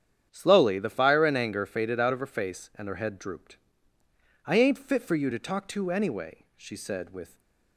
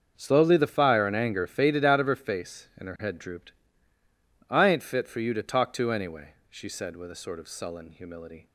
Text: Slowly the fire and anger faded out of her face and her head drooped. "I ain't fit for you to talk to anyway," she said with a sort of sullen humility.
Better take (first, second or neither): second